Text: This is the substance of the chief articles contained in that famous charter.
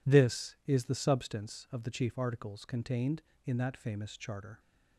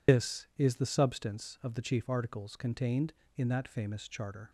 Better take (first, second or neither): first